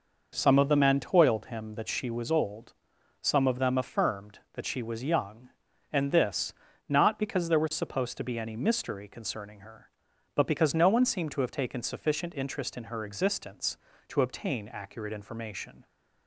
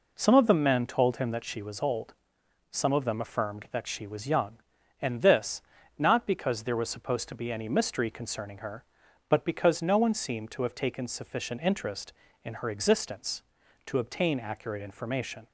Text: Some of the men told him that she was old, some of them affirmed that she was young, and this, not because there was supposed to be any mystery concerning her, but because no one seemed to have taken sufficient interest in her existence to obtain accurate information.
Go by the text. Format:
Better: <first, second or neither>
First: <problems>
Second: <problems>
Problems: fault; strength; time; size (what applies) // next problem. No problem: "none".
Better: second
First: says "toiled" for "told"; at 0.9 s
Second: none